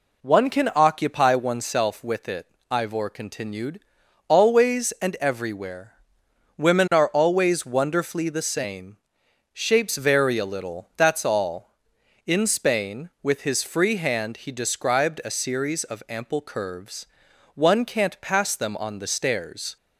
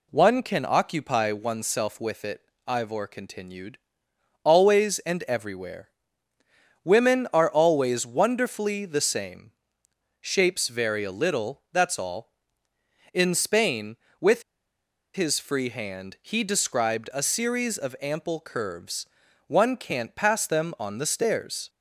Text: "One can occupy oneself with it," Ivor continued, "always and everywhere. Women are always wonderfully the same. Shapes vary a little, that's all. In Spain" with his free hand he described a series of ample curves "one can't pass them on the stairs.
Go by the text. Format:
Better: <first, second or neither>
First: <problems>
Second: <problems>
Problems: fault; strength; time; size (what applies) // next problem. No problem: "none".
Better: first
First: pauses between "curves" and "one"; noticeable; at 17.0 s; 0.50 s long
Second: pauses between "with" and "his"; noticeable; at 14.4 s; 0.72 s long // pauses between "curves" and "one"; at 19.0 s; 0.42 s long